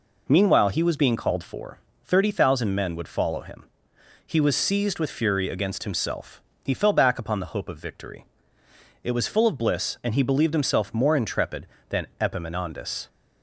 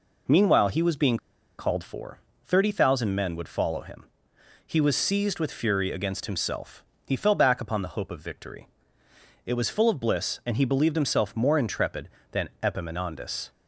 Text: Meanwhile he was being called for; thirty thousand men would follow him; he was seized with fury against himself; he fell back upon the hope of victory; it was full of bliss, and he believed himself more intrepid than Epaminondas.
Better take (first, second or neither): first